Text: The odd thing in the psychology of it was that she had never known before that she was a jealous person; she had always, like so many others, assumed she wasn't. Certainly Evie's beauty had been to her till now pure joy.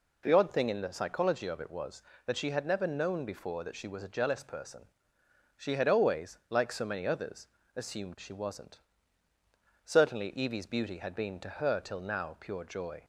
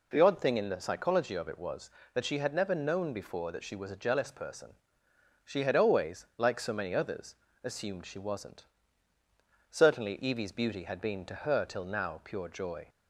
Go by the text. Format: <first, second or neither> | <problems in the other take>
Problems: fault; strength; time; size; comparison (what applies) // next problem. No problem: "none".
neither | none